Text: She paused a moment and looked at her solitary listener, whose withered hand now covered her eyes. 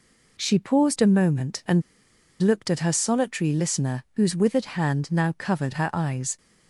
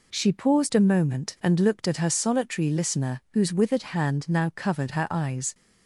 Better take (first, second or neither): second